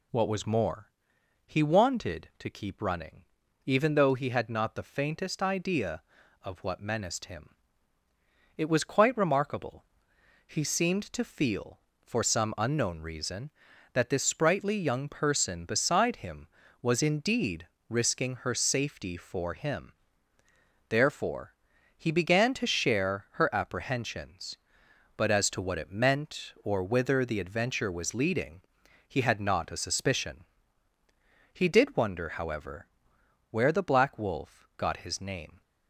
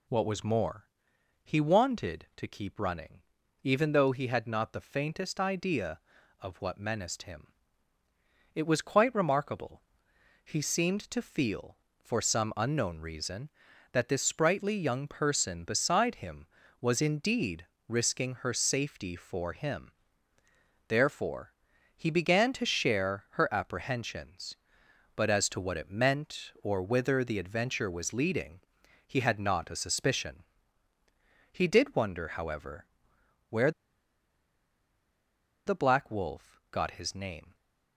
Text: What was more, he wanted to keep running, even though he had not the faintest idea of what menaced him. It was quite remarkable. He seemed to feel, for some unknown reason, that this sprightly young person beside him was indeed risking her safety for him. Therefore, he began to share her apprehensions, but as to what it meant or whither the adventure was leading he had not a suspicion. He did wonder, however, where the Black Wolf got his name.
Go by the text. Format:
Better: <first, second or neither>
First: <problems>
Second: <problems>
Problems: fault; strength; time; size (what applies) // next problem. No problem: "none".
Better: first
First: pauses between "indeed" and "risking"; slight; at 17.6 s; 0.20 s long // pauses between "leading" and "he"; noticeable; at 28.6 s; 0.50 s long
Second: pauses between "indeed" and "risking"; slight; at 17.6 s; 0.20 s long // pauses between "leading" and "he"; noticeable; at 28.6 s; 0.50 s long // pauses between "where" and "the"; strong; at 33.7 s; 1.9 s long